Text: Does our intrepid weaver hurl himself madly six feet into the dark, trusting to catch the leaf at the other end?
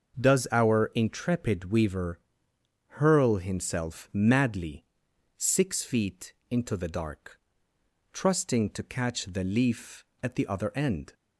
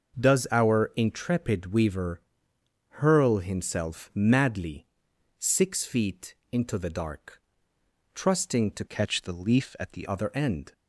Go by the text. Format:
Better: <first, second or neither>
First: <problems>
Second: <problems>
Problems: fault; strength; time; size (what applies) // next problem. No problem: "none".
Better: first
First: starts louder than the rest; until 1.2 s; 6.5 dB // pauses between "weaver" and "hurl"; noticeable; at 2.1 s; 0.66 s long // pauses between "madly" and "six"; noticeable; at 4.8 s; 0.52 s long // pauses between "feet" and "into"; slight; at 6.3 s; 0.18 s long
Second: starts louder than the rest; noticeable; until 1.2 s; 6 dB // pauses between "weaver" and "hurl"; noticeable; at 2.2 s; 0.66 s long // pauses between "madly" and "six"; noticeable; at 4.8 s; 0.52 s long // pauses between "feet" and "into"; slight; at 6.3 s; 0.18 s long // changes voice from "catch" to "the"; from 8.8 to 10.0 s; 1.2 s long